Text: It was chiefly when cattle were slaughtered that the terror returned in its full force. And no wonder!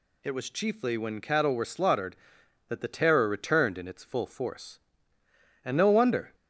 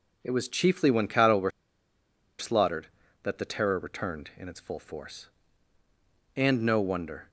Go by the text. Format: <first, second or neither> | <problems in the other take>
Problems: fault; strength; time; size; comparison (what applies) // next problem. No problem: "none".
first | pauses between "were" and "slaughtered"; noticeable; at 1.5 s; 0.88 s long